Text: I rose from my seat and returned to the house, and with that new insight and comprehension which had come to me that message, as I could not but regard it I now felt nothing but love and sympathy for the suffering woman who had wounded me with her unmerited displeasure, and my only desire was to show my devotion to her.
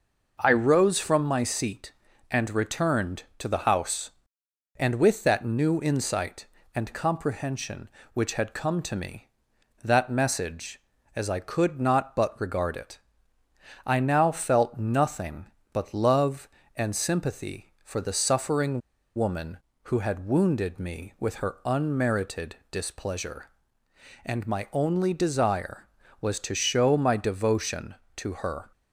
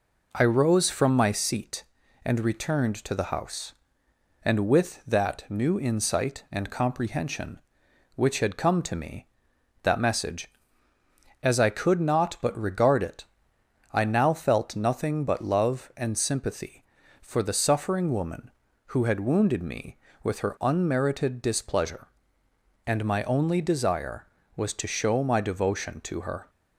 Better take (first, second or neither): second